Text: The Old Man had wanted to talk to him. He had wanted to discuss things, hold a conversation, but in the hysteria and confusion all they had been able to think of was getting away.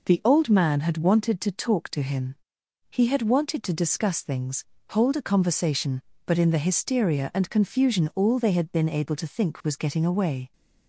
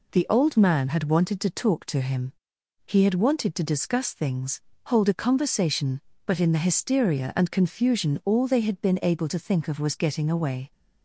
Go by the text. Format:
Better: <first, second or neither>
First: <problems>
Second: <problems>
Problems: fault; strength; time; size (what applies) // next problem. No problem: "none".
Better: second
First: skips "of"; at 9.6 s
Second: none